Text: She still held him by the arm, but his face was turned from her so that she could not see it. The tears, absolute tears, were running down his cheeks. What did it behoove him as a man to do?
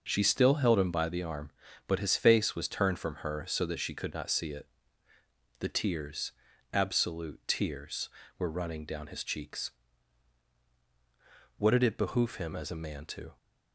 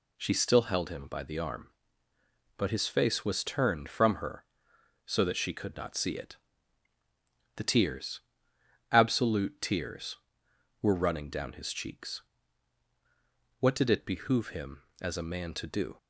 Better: second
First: stops before "do"; at 13.3 s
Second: none

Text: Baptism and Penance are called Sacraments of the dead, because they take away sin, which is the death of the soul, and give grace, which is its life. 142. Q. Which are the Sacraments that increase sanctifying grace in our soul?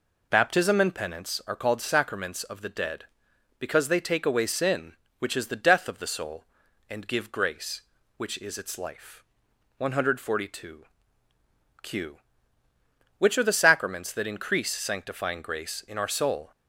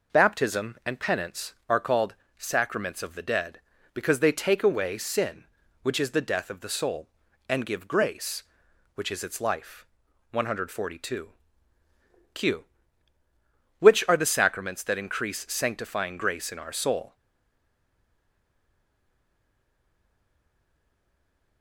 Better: first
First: none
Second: pauses between "called" and "Sacraments"; slight; at 2.1 s; 0.24 s long // stays silent after the last word; strong; from 17.1 s on; 4.5 s long

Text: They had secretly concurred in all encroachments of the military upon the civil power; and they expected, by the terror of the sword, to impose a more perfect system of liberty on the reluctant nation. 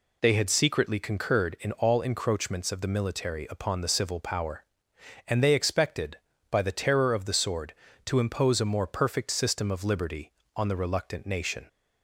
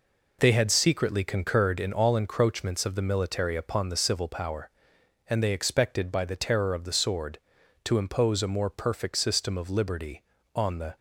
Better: first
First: none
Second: stops before "reluctant nation"; at 10.9 s

